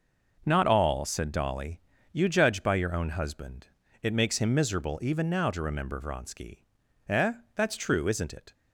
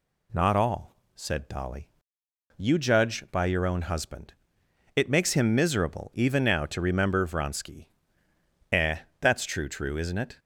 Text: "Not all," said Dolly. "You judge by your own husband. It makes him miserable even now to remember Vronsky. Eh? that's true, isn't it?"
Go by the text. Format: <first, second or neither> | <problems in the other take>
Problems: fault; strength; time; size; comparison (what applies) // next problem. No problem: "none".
first | says "true" twice; at 9.6 s